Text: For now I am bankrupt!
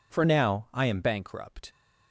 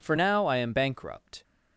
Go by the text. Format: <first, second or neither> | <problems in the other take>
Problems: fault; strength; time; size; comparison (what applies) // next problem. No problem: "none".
second | changes voice from "now" to "am"; from 0.2 to 1.0 s; 0.8 s long